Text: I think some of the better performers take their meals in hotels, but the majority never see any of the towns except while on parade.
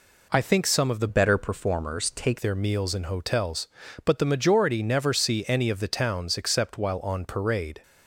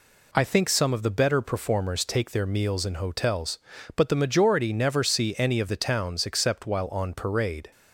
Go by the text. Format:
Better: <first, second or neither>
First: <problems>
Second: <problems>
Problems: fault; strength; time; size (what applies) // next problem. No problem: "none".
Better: second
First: changes voice from "better" to "take"; from 1.0 to 2.3 s; 1.3 s long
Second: none